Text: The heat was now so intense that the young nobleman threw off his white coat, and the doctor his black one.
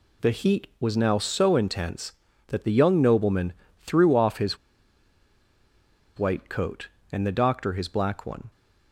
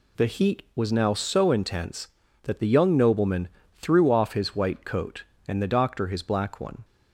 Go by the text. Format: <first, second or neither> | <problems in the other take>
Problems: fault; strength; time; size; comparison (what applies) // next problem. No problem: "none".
second | pauses between "nobleman" and "threw"; slight; at 3.5 s; 0.26 s long; slight in the second // pauses between "his" and "white"; strong; at 4.5 s; 1.6 s long